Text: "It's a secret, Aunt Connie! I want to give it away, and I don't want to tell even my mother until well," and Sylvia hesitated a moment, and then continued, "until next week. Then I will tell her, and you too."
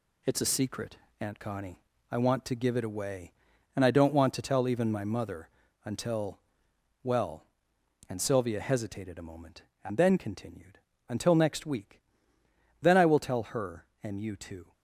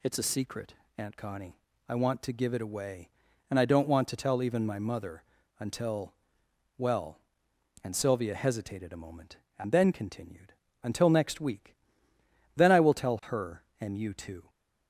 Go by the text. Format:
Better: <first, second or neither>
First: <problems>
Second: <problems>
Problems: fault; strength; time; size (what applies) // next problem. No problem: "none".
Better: second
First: gets quieter; noticeable; throughout; 5.5 dB // pauses between "mother" and "until"; slight; at 5.4 s; 0.34 s long // pauses between "until" and "well"; noticeable; at 6.3 s; 0.64 s long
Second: pauses between "mother" and "until"; slight; at 5.2 s; 0.34 s long // pauses between "until" and "well"; noticeable; at 6.1 s; 0.64 s long